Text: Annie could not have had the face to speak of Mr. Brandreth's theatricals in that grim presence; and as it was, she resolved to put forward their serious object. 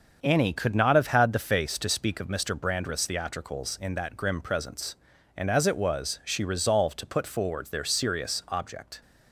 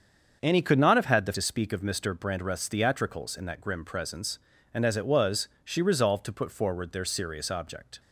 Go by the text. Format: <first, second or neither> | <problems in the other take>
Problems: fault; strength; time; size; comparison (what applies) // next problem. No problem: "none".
first | starts louder than the rest; until 1.4 s; 7 dB; also in the first // skips "face"; at 1.3 s